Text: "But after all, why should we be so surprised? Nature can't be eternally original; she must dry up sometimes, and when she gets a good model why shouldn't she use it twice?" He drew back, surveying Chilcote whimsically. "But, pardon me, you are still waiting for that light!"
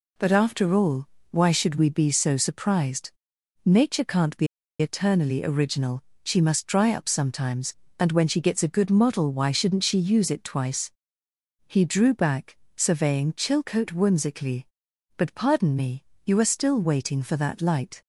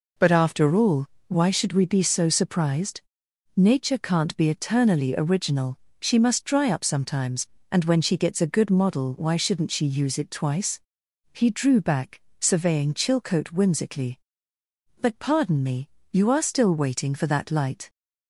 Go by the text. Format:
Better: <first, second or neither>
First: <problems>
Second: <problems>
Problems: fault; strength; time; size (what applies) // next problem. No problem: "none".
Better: second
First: pauses between "be" and "eternally"; slight; at 4.4 s; 0.34 s long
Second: none